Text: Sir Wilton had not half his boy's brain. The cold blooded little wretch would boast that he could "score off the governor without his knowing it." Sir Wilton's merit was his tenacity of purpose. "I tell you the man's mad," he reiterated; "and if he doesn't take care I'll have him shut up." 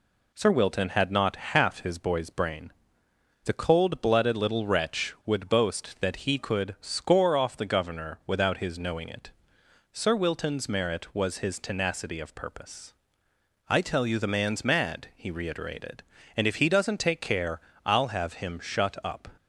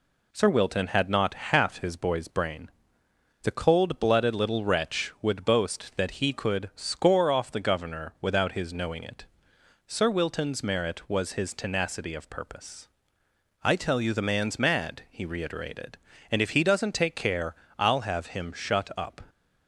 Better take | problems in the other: neither | pauses between "care" and "I'll"; slight; the same in both

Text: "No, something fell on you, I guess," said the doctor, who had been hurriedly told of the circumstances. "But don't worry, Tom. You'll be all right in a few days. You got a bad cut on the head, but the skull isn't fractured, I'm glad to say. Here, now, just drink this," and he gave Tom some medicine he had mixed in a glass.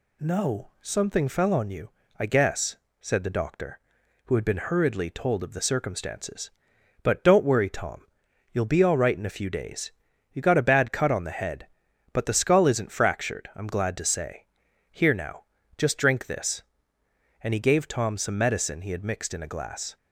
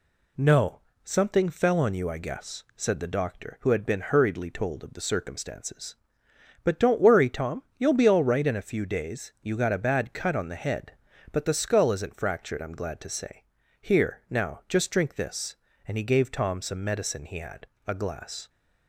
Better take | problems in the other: first | skips "mixed in"; at 17.7 s

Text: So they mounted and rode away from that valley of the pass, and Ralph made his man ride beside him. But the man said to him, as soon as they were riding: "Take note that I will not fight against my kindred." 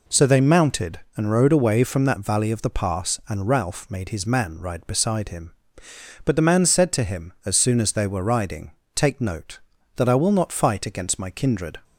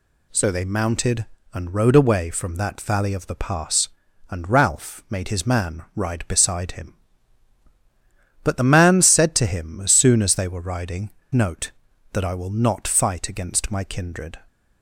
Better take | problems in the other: first | skips "Take"; at 11.2 s

